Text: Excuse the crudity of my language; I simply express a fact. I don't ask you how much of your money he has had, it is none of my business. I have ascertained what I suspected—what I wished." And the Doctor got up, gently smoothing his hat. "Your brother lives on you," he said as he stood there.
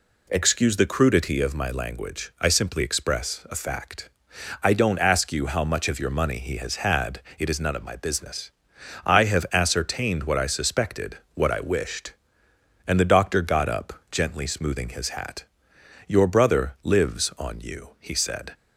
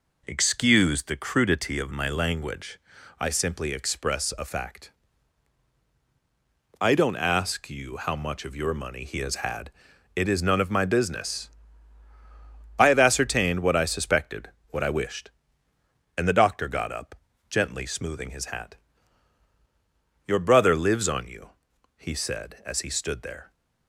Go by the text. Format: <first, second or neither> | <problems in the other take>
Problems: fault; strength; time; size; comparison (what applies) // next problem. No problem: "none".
second | stops before "as he stood there"; at 18.5 s